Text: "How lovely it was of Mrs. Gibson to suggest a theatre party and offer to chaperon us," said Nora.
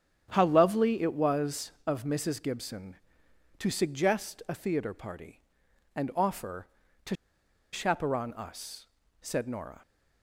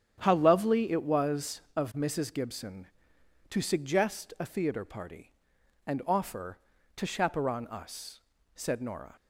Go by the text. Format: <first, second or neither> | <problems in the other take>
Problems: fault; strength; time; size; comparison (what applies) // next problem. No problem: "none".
second | starts louder than the rest; strong; until 1.3 s; 9 dB; strong in the second // pauses between "to" and "chaperon"; noticeable; at 7.1 s; 0.57 s long